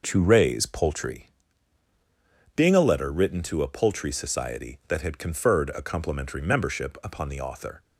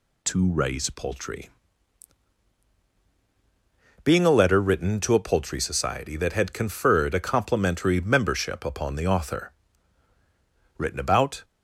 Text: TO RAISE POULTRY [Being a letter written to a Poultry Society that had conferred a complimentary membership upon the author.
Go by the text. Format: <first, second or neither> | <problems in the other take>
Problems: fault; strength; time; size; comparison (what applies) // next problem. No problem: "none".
first | pauses between "POULTRY" and "Being"; strong; at 1.4 s; 2.5 s long; strong in the first // goes on to say "Written about"; noticeable; from 10.7 s on; 0.66 s long